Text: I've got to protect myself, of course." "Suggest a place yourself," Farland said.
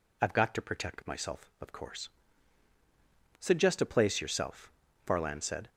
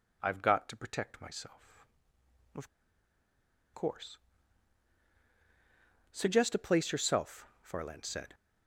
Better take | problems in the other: first | pauses between "of" and "course"; at 2.6 s; 1.0 s long

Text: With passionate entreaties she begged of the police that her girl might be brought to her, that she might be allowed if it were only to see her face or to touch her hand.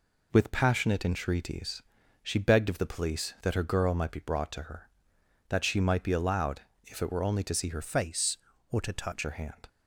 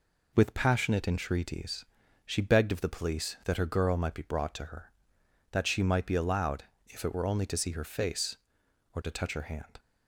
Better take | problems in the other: second | pauses between "entreaties" and "she"; at 1.8 s; 0.40 s long; also in the second // pauses between "allowed" and "if"; slight; at 6.6 s; 0.26 s long; slight in the second // changes voice from "face" to "touch"; from 7.8 to 9.2 s; 1.4 s long

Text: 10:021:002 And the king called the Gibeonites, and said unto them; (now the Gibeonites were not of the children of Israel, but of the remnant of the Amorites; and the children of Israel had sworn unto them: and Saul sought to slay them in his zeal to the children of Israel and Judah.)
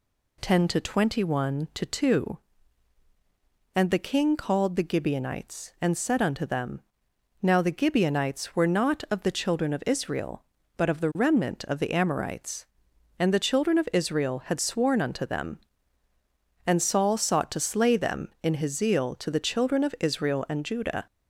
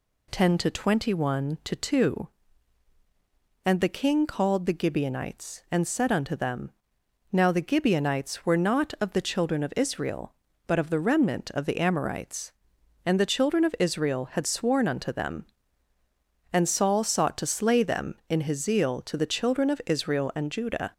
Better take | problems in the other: neither | none

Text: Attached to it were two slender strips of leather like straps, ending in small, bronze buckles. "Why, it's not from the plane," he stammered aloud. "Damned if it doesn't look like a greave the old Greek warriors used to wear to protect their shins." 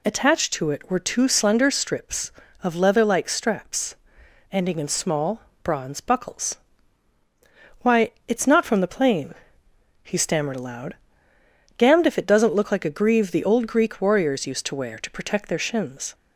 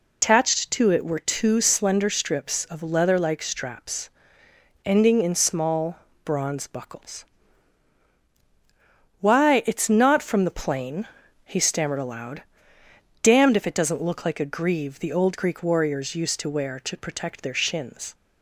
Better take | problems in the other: first | loses the start of "Attached"; at 0.2 s; 135 ms

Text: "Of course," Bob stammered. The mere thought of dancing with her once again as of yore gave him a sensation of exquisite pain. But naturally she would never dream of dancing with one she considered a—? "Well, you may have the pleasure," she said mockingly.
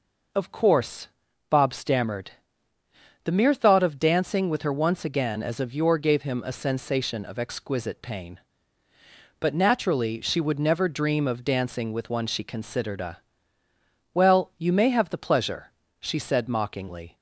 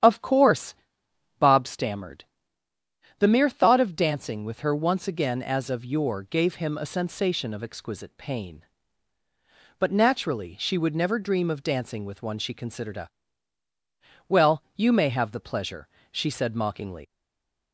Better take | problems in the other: first | starts louder than the rest; strong; until 1.6 s; 9.5 dB // stays silent after the last word; slight; from 17.0 s on; 0.7 s long

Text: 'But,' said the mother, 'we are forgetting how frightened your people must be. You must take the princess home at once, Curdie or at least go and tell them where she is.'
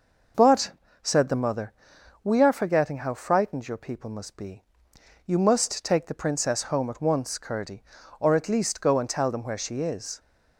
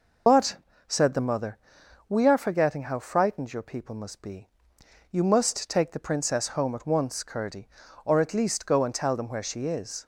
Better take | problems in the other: first | loses the start of "But"; at 0.2 s; 55 ms

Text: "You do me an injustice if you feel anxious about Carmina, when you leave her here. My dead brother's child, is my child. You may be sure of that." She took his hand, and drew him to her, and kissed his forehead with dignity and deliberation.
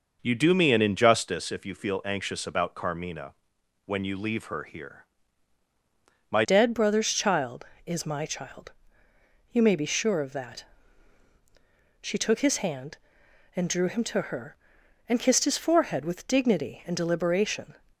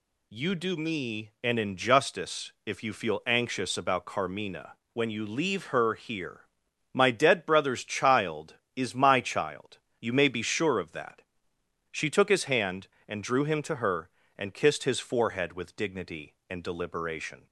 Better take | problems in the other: second | changes voice at "dead"; from 6.4 s on; 11.3 s long

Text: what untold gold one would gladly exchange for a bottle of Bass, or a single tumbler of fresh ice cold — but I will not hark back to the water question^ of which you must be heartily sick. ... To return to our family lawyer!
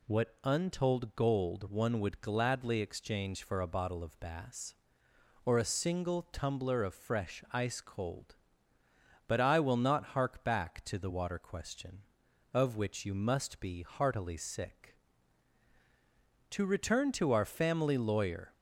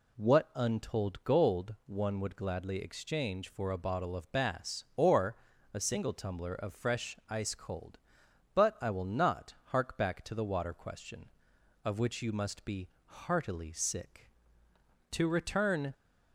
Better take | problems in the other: first | pauses between "or" and "a"; at 5.3 s; 0.38 s long // pauses between "be" and "heartily"; slight; at 12.8 s; 0.16 s long // stops before "to our family lawyer"; at 15.9 s

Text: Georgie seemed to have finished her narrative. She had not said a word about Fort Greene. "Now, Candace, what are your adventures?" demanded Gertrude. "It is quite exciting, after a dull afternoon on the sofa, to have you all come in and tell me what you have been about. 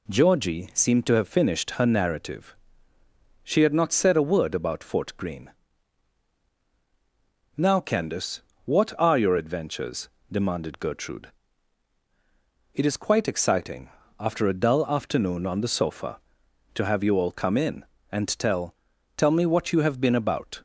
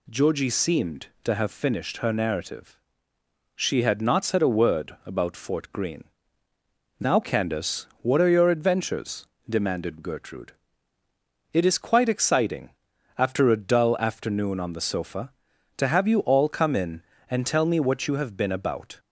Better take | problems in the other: second | says "tell" twice; at 19.1 s

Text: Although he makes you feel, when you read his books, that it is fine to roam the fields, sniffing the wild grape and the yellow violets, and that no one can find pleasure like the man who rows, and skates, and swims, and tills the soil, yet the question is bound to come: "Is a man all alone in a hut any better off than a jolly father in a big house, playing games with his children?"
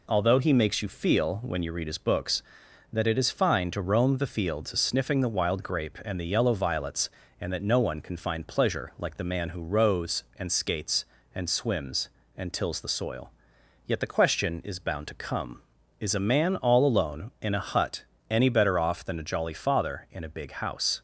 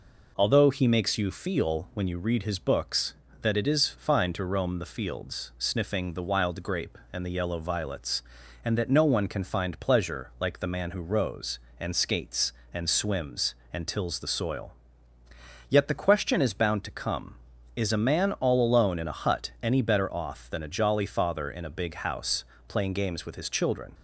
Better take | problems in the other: second | pauses between "hut" and "any"; slight; at 18.0 s; 0.26 s long // stops before "playing games with his children"; at 20.9 s

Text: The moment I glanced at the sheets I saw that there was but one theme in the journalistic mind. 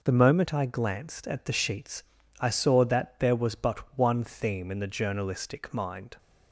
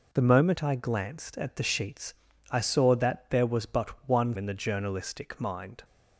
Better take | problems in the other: first | pauses between "sheets" and "I"; slight; at 2.1 s; 0.36 s long; slight in the first // skips "theme"; at 4.3 s

